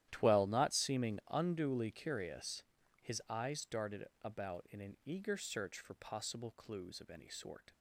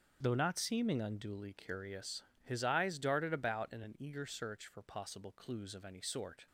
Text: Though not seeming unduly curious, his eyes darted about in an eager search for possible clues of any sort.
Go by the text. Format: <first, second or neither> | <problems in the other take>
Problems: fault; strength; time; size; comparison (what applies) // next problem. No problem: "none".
second | starts louder than the rest; strong; until 1.1 s; 12 dB; also in the second // says "Twell" for "Though"; at 0.1 s // pauses between "darted" and "about"; slight; at 4.0 s; 0.18 s long